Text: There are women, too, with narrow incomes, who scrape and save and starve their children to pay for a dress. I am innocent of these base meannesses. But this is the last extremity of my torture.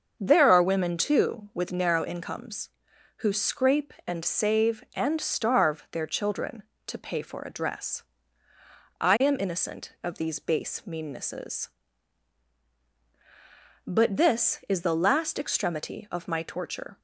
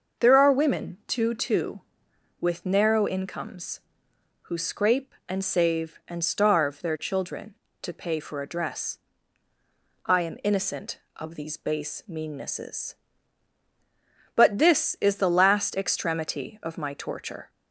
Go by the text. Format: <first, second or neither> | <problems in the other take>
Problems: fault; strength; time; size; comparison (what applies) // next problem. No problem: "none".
first | starts louder than the rest; noticeable; until 1.3 s; 6 dB; also in the first // says "too" twice; at 1.3 s